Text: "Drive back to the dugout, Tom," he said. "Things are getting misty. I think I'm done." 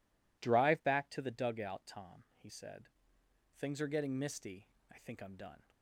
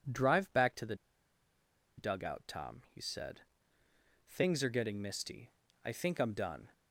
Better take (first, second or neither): first